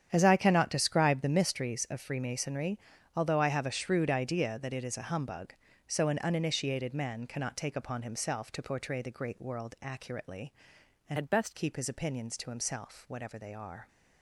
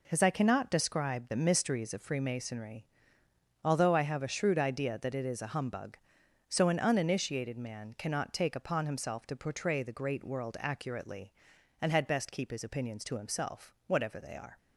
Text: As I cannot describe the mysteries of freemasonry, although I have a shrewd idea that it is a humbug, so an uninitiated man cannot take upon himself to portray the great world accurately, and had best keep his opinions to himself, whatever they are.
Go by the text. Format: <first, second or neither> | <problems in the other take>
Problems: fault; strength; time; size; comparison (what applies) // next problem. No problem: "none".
second | starts louder than the rest; strong; until 1.1 s; 9 dB // changes voice from "had" to "best"; from 11.1 to 11.5 s; 0.4 s long